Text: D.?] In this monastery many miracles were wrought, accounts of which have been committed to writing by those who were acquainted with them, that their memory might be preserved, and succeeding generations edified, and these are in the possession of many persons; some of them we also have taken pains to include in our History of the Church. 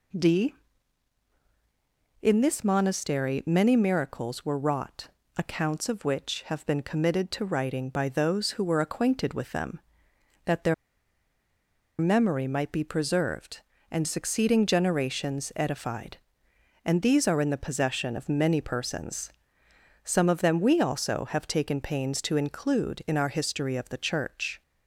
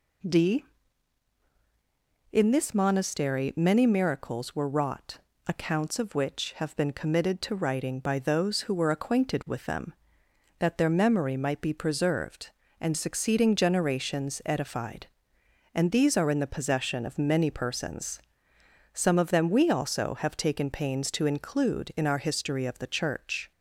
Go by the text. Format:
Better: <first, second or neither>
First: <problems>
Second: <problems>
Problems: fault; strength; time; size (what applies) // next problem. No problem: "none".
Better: second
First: pauses between "their" and "memory"; strong; at 10.7 s; 1.2 s long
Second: none